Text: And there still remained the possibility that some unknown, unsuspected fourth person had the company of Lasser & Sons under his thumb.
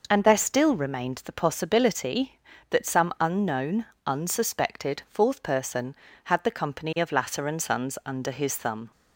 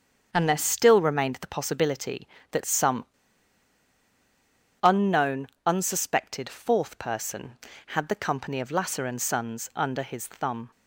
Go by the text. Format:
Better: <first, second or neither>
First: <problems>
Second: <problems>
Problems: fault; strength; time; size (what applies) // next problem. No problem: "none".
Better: first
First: none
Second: starts louder than the rest; until 1.3 s; 7 dB // pauses between "some" and "unknown"; strong; at 3.0 s; 1.7 s long